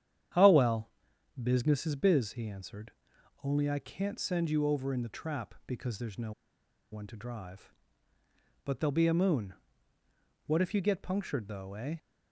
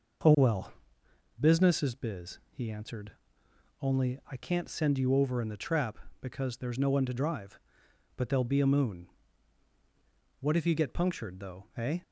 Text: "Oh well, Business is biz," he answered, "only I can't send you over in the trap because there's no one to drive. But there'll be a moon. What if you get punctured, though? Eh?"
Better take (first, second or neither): second